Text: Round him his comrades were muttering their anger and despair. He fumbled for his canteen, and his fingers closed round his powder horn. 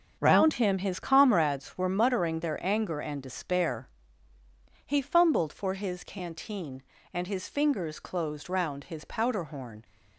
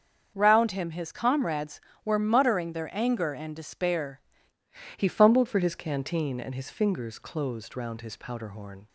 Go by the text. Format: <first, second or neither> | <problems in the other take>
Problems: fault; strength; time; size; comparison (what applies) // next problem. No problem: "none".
first | starts louder than the rest; until 1.3 s; 7 dB; also in the first // changes voice at "He"; from 4.9 s on; 3.9 s long